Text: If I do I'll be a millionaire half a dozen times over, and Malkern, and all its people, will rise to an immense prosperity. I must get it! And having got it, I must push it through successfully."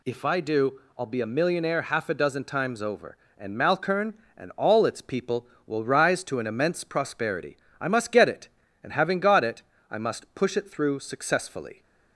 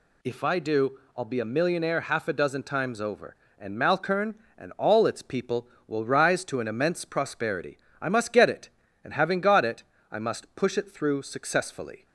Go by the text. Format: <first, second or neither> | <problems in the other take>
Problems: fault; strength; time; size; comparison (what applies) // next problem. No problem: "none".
neither | pauses between "do" and "I'll"; slight; the same in both